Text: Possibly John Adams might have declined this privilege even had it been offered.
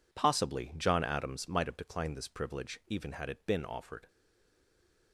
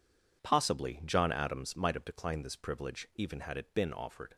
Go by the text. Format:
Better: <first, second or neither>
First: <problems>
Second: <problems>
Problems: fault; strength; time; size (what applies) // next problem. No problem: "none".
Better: second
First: stays silent after the last word; from 4.0 s on; 1.1 s long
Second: none